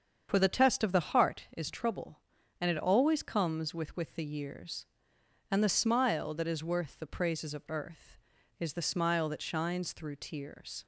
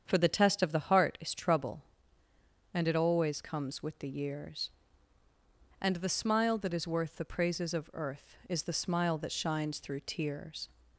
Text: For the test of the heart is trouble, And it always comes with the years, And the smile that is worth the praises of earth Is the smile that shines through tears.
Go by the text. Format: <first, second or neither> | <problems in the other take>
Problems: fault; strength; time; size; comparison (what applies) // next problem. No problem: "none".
second | starts louder than the rest; strong; until 1.3 s; 7 dB; strong in the second // says "with" twice; at 3.9 s